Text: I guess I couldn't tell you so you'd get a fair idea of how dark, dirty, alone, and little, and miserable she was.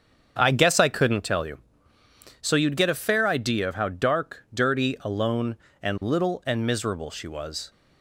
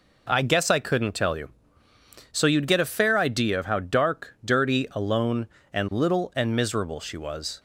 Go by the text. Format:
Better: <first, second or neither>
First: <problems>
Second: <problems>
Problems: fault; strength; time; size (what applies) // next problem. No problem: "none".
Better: second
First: starts louder than the rest; strong; until 1.3 s; 7.5 dB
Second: none